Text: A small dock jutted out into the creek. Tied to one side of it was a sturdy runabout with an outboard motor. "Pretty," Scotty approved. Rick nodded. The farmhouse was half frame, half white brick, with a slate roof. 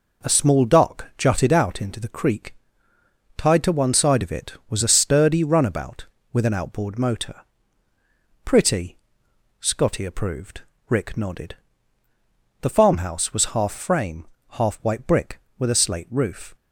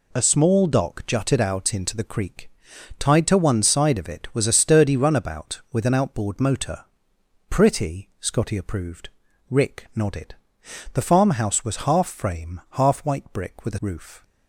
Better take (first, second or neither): first